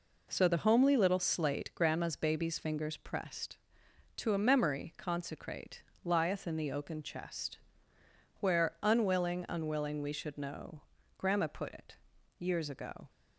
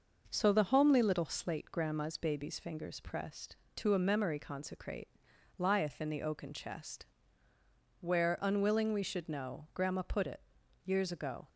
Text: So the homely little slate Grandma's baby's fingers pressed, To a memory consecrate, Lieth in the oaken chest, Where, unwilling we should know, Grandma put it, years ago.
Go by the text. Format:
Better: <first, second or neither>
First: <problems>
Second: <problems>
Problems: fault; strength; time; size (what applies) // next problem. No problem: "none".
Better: second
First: says "unwilling" twice; at 9.4 s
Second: none